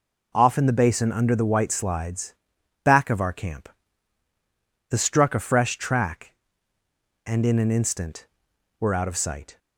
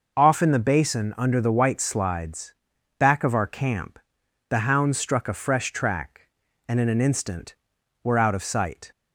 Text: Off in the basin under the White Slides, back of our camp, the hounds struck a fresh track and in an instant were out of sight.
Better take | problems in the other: second | skips "hounds"; at 4.9 s

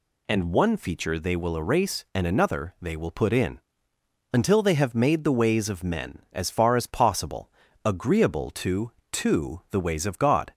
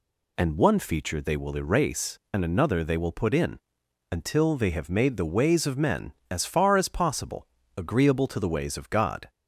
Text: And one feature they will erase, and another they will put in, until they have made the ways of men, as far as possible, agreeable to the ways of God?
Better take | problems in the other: second | says "to" twice; at 9.1 s

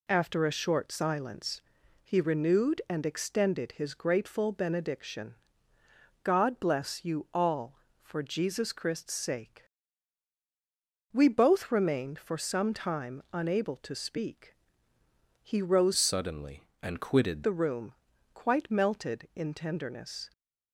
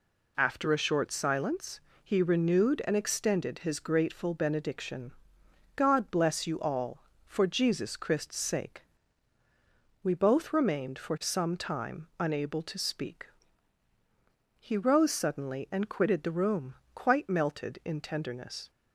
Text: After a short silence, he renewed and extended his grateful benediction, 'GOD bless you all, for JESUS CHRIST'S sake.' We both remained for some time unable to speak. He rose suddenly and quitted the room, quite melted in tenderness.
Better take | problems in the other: second | changes voice from "suddenly" to "quitted"; from 15.9 to 17.4 s; 1.5 s long

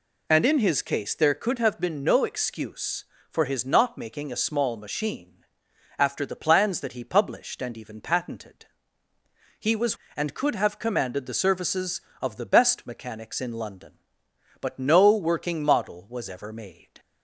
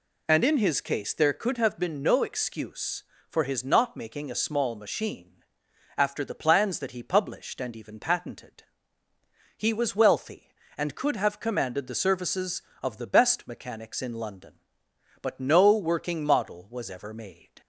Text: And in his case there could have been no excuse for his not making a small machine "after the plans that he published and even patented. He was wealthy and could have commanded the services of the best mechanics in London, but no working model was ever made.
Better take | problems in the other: second | pauses between "machine" and "after"; noticeable; at 5.4 s; 0.52 s long; noticeable in the second // skips "wealthy"; at 10.0 s

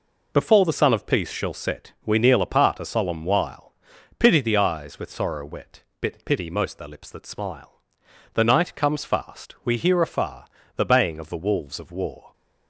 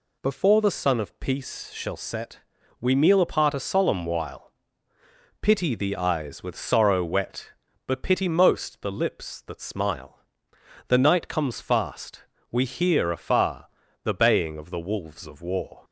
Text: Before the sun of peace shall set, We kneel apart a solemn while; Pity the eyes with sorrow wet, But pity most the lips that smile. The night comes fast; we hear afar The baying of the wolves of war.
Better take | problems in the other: second | says "Bit" for "But"; at 6.0 s // pauses between "afar" and "The"; slight; at 10.4 s; 0.30 s long; slight in the second

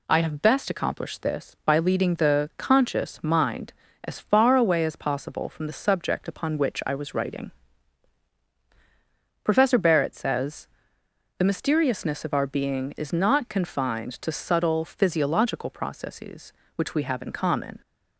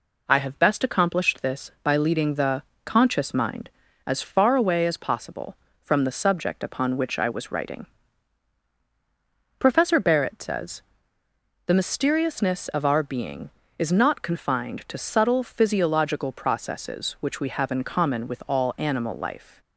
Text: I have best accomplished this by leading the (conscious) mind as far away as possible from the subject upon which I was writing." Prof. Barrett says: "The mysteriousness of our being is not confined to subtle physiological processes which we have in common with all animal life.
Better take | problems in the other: second | stops before "with all animal life"; at 17.8 s

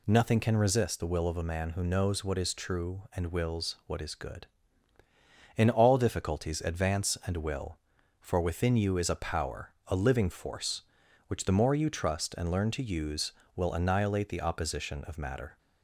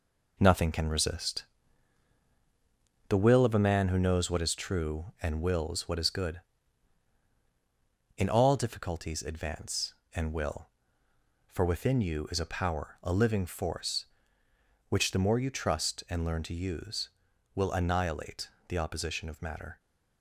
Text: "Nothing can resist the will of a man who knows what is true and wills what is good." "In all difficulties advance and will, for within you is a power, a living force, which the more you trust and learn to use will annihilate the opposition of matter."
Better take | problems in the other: first | gets quieter; throughout; 6.5 dB // pauses between "resist" and "the"; strong; at 1.4 s; 1.6 s long // pauses between "annihilate" and "the"; slight; at 18.4 s; 0.18 s long

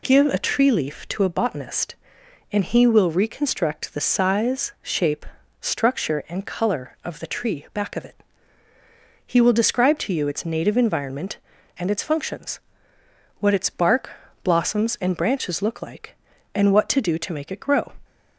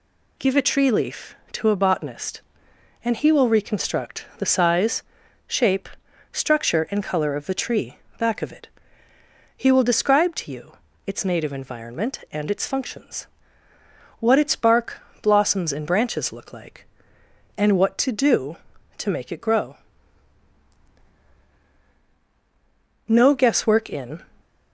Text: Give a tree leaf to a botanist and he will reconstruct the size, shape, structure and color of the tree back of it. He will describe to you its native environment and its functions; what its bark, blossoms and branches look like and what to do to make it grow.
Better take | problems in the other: first | pauses between "tree" and "back"; slight; at 7.9 s; 0.22 s long // pauses between "you" and "its"; slight; at 10.7 s; 0.34 s long // goes on to say "No Guesswork in"; noticeable; from 23.0 s on; 1.1 s long

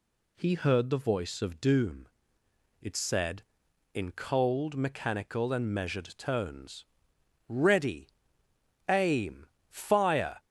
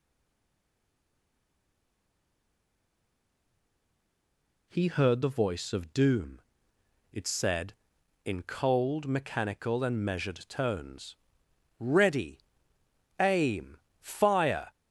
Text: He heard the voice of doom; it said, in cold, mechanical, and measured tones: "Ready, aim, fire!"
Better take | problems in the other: first | stays silent before the first word; strong; until 4.6 s; 4.6 s long

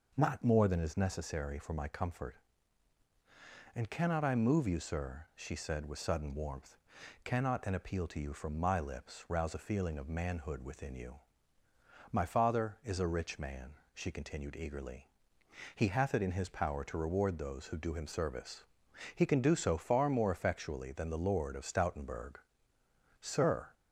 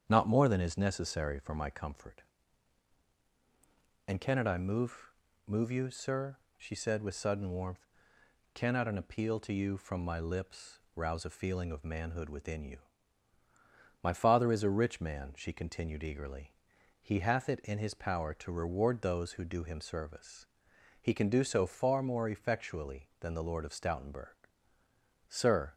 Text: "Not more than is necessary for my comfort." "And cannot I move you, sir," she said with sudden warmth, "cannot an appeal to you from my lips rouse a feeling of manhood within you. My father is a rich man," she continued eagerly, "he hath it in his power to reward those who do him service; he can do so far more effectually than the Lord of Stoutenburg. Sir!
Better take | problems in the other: first | starts louder than the rest; strong; until 1.0 s; 8 dB // says "move" twice; at 5.4 s // pauses between "lips" and "rouse"; slight; at 10.7 s; 0.16 s long

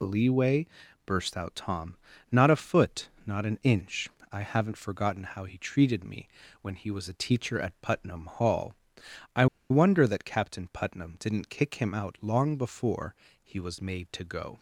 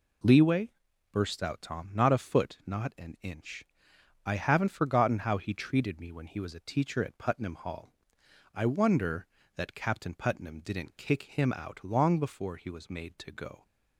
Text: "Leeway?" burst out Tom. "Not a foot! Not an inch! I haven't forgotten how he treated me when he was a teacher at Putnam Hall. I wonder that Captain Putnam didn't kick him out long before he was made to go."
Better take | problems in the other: second | pauses between "me" and "when"; slight; at 6.2 s; 0.34 s long // pauses between "I" and "wonder"; slight; at 9.4 s; 0.24 s long // pauses between "before" and "he"; slight; at 13.1 s; 0.30 s long

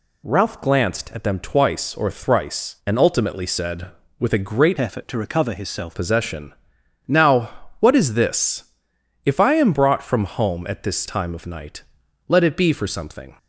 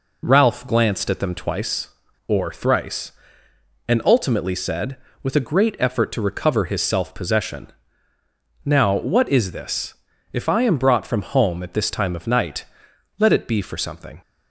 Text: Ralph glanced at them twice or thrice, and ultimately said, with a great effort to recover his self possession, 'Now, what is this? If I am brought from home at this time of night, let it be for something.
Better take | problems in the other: second | changes voice from "effort" to "self"; from 4.8 to 5.9 s; 1.1 s long

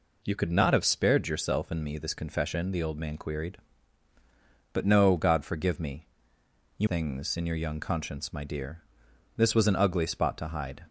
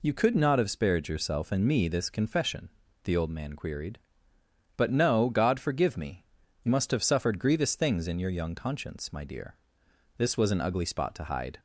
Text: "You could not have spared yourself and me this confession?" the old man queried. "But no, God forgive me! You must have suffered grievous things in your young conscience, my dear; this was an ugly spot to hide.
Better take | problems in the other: second | skips "must have suffered grievous"; at 6.8 s

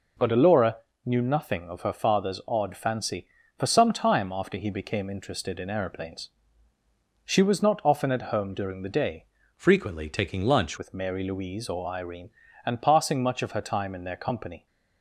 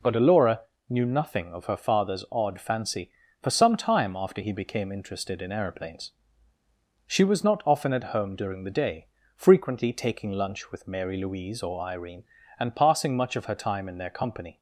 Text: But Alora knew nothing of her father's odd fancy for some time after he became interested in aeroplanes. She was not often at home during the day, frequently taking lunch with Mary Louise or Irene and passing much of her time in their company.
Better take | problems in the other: second | pauses between "Alora" and "knew"; slight; at 0.7 s; 0.28 s long; slight in the second // changes voice from "frequently" to "lunch"; from 9.5 to 10.7 s; 1.2 s long

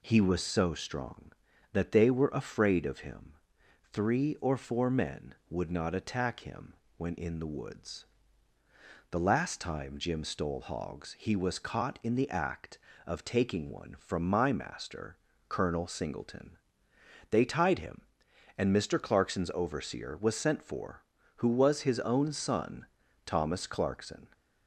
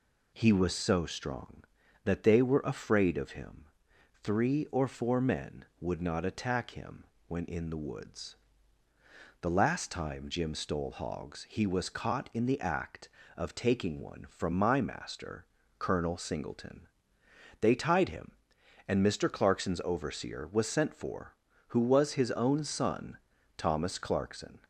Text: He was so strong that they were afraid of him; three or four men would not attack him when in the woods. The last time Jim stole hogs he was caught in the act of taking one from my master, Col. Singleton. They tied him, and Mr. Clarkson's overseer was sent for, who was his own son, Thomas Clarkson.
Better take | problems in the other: neither | pauses between "him" and "when"; slight; the same in both

